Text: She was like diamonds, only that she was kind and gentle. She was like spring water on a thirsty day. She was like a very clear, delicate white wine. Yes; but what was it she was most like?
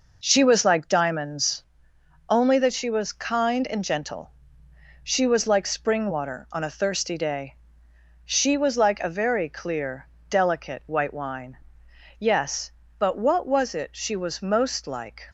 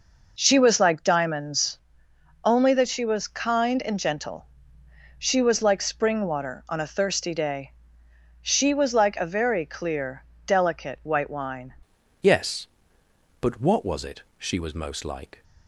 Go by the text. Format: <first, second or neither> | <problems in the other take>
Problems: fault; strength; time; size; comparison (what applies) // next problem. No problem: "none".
first | changes voice at "Yes"; from 12.2 s on; 3.2 s long // pauses between "it" and "she"; slight; at 14.2 s; 0.16 s long